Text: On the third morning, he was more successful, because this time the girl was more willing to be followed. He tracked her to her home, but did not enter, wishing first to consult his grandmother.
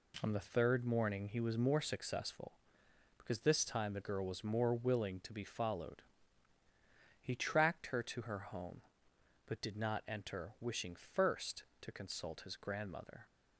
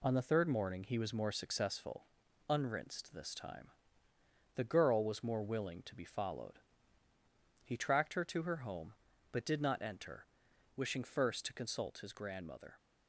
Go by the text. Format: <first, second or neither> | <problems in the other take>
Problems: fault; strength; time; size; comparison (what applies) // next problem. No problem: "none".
first | says "unrinsed" for "because"; at 2.4 s // pauses between "time" and "the"; noticeable; at 3.6 s; 0.86 s long